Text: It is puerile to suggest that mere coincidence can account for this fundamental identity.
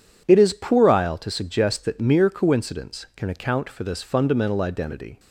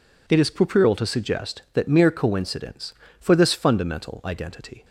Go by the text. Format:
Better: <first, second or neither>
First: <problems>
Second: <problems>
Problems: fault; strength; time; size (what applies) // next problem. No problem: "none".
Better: first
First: none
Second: skips "can account"; at 3.0 s